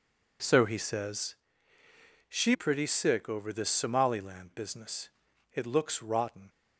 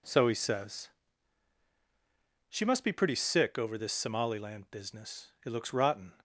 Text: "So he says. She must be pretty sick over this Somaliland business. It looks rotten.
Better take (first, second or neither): second